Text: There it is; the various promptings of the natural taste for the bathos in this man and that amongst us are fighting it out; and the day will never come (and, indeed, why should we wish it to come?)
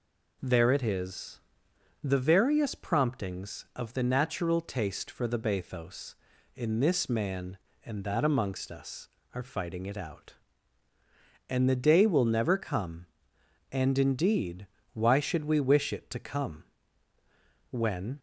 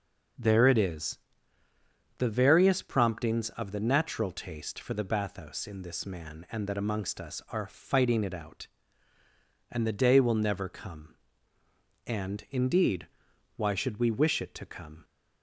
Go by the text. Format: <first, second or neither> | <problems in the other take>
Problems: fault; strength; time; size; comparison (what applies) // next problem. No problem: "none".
second | goes on to say "when"; from 17.6 s on; 0.50 s long